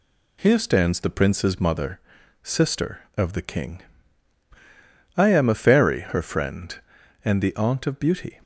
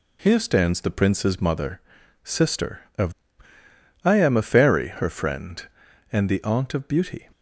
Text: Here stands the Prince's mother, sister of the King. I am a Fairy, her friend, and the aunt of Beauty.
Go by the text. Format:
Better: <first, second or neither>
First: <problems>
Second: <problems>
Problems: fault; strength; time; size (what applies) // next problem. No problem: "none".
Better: first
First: none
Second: skips "the King"; at 3.5 s